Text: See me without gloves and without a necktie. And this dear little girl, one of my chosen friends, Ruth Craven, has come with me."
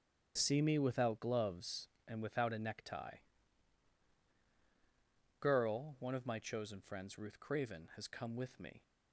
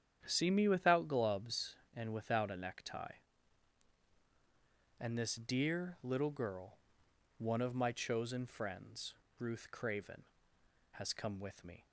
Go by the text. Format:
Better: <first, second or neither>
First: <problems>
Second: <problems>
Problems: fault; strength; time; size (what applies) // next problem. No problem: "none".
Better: second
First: starts louder than the rest; strong; until 1.3 s; 9 dB // skips "And this dear little"; at 4.3 s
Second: starts louder than the rest; strong; until 1.2 s; 9 dB